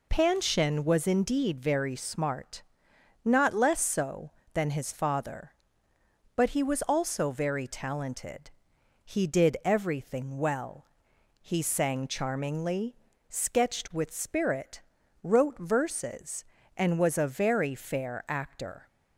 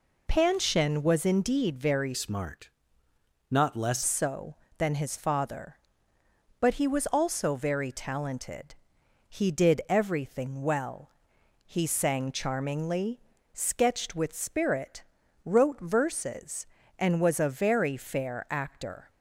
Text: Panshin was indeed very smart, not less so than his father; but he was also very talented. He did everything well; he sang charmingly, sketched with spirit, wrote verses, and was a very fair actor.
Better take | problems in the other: first | changes voice from "smart" to "less"; from 2.1 to 4.0 s; 1.9 s long

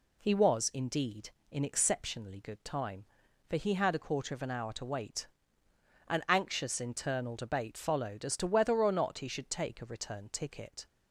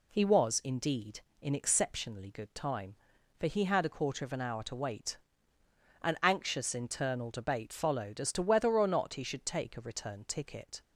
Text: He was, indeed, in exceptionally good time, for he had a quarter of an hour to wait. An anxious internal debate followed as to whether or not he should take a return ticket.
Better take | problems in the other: neither | none

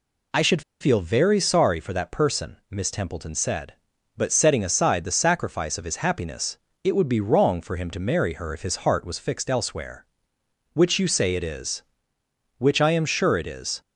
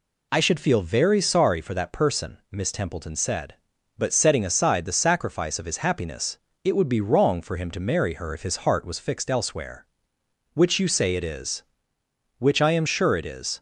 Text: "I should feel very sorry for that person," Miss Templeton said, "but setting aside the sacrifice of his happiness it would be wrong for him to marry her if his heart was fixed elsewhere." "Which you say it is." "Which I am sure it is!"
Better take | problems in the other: second | pauses between "should" and "feel"; slight; at 0.6 s; 0.19 s long // pauses between "happiness" and "it"; slight; at 6.5 s; 0.24 s long; slight in the second

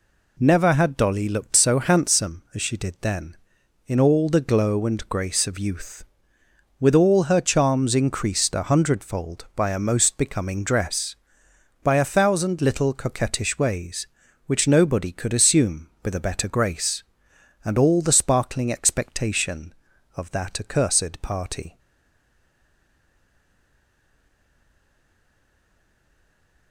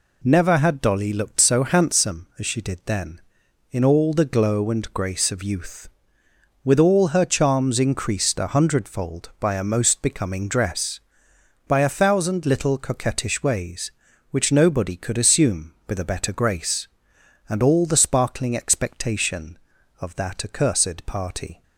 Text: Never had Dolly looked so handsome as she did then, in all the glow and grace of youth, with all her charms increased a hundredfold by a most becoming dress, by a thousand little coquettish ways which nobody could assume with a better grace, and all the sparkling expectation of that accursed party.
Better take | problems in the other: second | stays silent after the last word; strong; from 21.7 s on; 5.0 s long

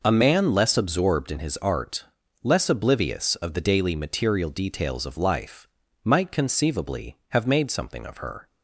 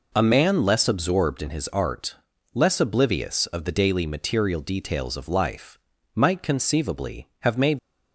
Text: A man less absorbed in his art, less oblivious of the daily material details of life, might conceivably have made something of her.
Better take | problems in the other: first | stops before "something of her"; at 7.7 s

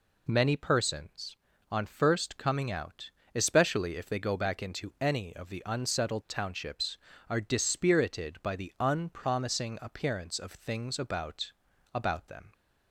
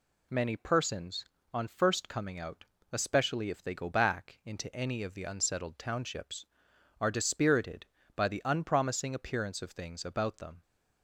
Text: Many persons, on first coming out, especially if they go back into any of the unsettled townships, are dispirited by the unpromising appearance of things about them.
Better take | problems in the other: second | says "about" twice; at 11.9 s

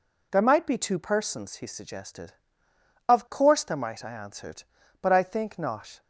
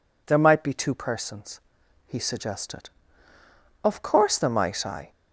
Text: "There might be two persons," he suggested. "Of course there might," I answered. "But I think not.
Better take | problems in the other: first | stops before "answered But I think not"; at 5.1 s

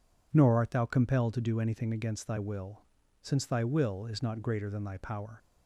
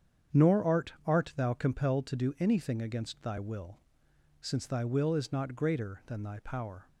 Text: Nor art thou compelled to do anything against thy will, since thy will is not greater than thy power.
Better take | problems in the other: first | starts louder than the rest; strong; until 1.5 s; 8 dB // says "art" twice; at 1.0 s

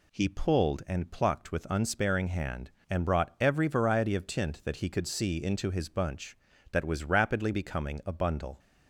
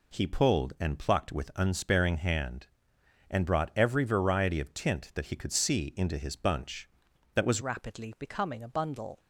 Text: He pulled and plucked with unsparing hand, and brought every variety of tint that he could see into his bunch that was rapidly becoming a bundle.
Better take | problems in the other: first | changes voice at "rapidly"; from 7.6 s on; 1.5 s long

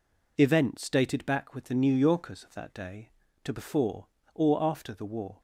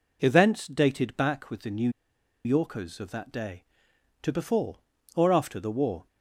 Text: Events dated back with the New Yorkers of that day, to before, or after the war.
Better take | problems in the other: first | pauses between "New" and "Yorkers"; noticeable; at 1.8 s; 0.55 s long

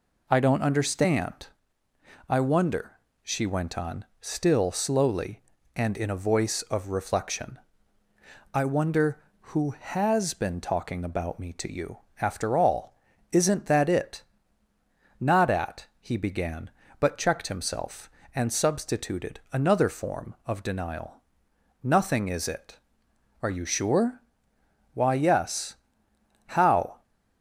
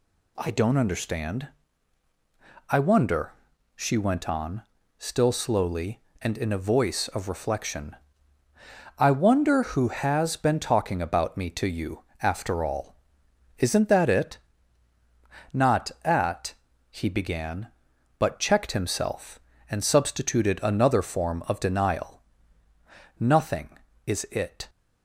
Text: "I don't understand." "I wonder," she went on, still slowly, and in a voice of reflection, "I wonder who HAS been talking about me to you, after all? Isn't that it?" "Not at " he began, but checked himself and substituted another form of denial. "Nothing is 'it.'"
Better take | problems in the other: second | goes on to say "Are you sure Why yes How"; strong; from 23.4 s on; 3.5 s long

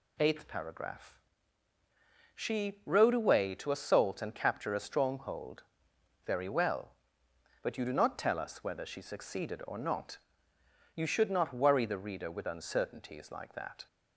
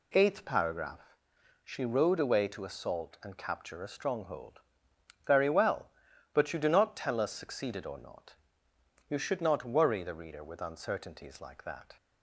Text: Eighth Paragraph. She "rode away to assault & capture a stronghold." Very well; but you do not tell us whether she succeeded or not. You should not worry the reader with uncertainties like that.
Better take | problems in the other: first | skips "whether she"; at 7.3 s

